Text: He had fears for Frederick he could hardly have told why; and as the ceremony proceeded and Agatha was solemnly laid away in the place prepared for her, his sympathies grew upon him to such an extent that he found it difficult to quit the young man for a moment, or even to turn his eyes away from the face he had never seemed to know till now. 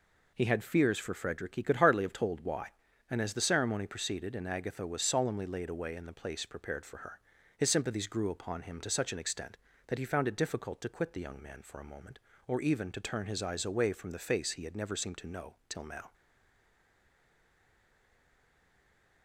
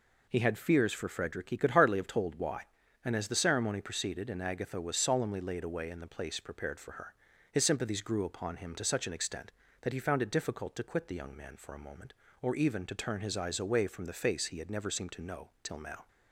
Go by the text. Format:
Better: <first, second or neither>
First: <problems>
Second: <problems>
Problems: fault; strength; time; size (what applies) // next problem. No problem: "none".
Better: second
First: stays silent after the last word; strong; from 16.1 s on; 3.1 s long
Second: none